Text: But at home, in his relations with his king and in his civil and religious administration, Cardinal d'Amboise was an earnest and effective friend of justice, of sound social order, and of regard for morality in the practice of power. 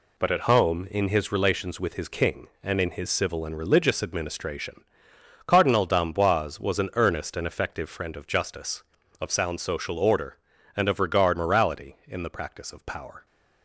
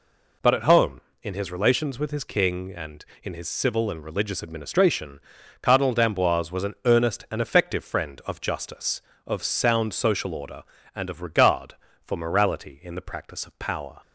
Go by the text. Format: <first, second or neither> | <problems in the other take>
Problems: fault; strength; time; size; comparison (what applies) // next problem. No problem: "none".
second | skips "for"; at 11.3 s